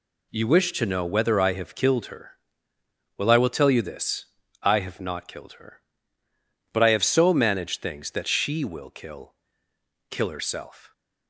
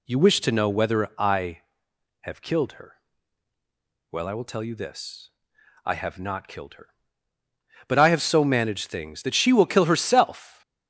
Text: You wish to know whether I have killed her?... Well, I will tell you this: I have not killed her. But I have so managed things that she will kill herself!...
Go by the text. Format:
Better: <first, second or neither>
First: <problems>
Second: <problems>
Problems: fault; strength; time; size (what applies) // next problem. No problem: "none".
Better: second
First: says "kill" twice; at 10.1 s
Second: none